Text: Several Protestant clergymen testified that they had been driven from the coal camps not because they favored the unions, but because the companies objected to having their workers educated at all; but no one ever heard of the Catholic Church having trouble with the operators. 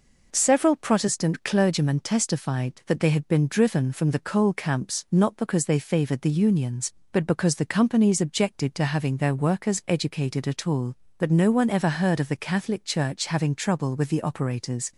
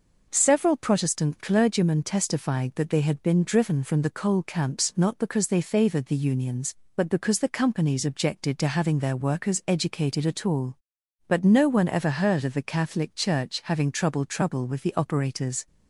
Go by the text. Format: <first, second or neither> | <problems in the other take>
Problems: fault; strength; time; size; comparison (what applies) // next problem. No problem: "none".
first | says "trouble" twice; at 14.2 s